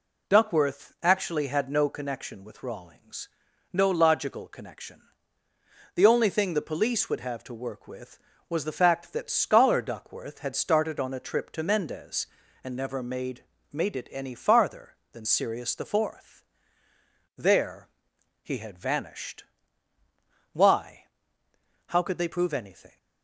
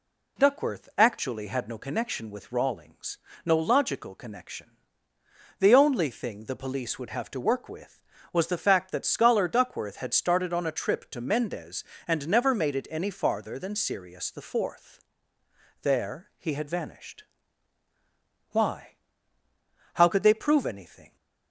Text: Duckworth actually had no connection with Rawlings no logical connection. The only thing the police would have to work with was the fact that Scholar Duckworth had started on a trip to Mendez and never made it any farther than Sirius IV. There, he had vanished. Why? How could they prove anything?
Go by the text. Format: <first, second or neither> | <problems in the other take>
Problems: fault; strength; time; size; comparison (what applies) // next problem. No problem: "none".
second | pauses between "Rawlings" and "no"; noticeable; at 3.2 s; 0.46 s long; slight in the second // says "made" twice; at 13.7 s